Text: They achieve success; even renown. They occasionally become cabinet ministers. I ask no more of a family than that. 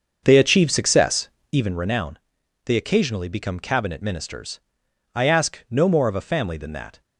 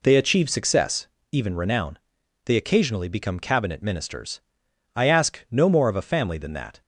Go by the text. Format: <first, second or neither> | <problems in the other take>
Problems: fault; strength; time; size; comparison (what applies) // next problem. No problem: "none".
second | starts louder than the rest; until 1.9 s; 6.5 dB